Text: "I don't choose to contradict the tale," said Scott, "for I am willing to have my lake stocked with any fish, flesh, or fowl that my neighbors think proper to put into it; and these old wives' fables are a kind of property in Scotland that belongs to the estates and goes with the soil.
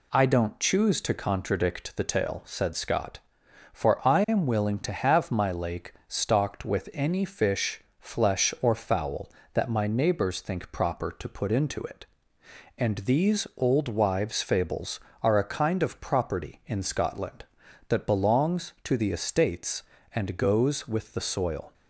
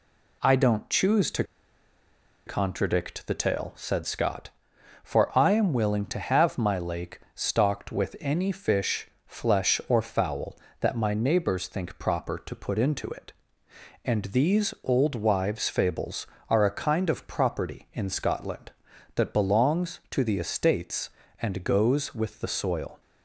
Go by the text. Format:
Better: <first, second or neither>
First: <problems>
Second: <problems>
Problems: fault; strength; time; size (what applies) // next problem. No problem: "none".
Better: first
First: none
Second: pauses between "to" and "contradict"; at 1.4 s; 1.0 s long